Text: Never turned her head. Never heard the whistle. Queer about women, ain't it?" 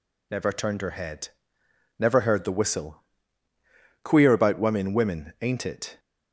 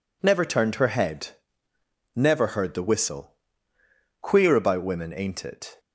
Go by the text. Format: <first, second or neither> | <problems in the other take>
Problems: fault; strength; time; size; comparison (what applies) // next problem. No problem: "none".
second | says "women" twice; at 4.9 s